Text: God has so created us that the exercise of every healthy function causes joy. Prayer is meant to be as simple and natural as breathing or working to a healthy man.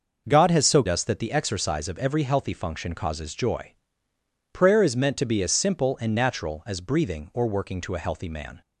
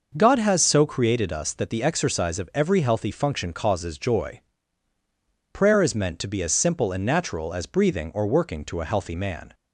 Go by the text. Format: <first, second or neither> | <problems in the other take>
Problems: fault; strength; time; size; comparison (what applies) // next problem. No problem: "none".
second | skips "created"; at 0.8 s